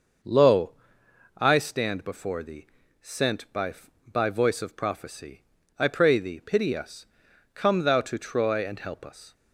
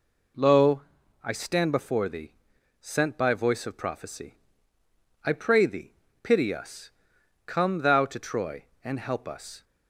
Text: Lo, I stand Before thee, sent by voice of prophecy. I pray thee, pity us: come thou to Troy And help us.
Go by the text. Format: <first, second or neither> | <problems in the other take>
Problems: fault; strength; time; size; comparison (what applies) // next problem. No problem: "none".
second | says "by" twice; at 4.1 s